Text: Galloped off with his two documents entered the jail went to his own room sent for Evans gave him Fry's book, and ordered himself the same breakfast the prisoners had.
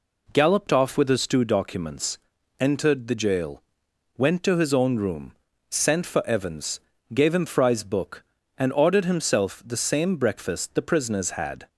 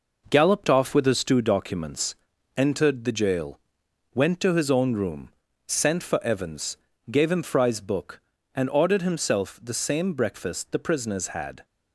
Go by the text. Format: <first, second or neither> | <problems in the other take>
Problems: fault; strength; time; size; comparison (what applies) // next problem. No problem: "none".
first | gets quieter; throughout; 6.5 dB // pauses between "documents" and "entered"; at 2.1 s; 0.42 s long; also in the first // pauses between "jail" and "went"; noticeable; at 3.5 s; 0.56 s long; noticeable in the first // pauses between "room" and "sent"; slight; at 5.3 s; 0.36 s long; slight in the first // pauses between "Evans" and "gave"; slight; at 6.7 s; 0.34 s long; slight in the first